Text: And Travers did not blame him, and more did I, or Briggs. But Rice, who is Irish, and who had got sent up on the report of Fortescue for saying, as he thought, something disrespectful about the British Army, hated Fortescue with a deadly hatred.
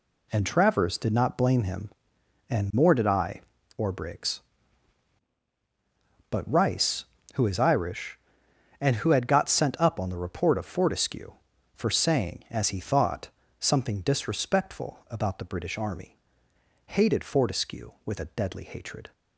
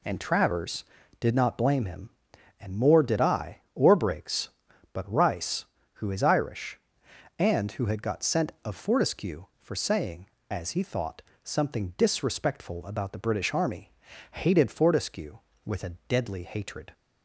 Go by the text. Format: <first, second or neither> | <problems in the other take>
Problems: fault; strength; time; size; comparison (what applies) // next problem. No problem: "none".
first | skips "up on the report"; at 8.5 s